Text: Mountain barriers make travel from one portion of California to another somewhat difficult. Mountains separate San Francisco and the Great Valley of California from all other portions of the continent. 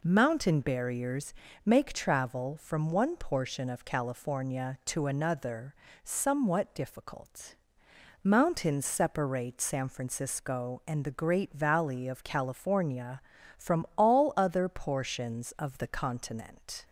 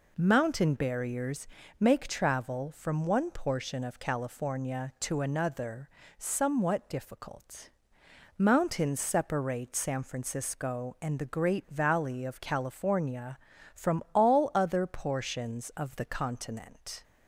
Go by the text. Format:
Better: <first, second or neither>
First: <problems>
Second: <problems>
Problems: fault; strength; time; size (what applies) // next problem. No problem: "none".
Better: neither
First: pauses between "barriers" and "make"; slight; at 1.3 s; 0.31 s long // pauses between "another" and "somewhat"; slight; at 5.7 s; 0.30 s long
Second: pauses between "barriers" and "make"; slight; at 1.4 s; 0.32 s long // pauses between "another" and "somewhat"; slight; at 5.8 s; 0.30 s long